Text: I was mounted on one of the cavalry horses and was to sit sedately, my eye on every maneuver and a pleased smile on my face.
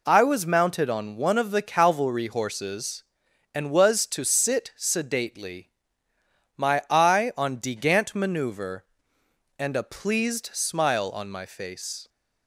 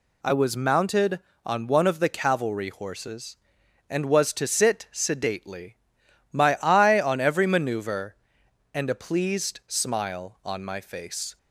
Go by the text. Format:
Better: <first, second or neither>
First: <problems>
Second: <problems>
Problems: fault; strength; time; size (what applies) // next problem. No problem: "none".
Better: second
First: says "degant" for "every"; at 7.5 s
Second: none